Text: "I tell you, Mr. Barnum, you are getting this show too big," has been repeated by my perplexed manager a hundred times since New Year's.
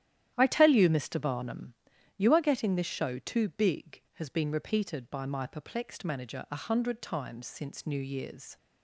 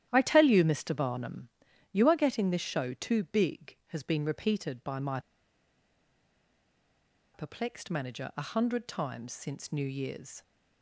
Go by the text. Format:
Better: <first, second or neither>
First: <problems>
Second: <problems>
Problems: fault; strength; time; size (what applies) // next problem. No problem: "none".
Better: first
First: starts louder than the rest; strong; until 1.3 s; 11.5 dB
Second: starts louder than the rest; strong; until 1.1 s; 11.5 dB // pauses between "my" and "perplexed"; strong; at 5.1 s; 2.1 s long